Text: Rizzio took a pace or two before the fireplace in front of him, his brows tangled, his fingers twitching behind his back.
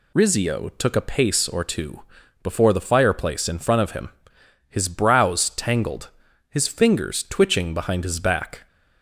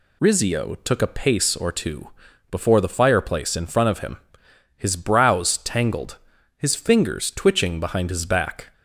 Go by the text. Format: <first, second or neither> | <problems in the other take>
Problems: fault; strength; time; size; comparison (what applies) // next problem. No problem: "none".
neither | pauses between "two" and "before"; the same in both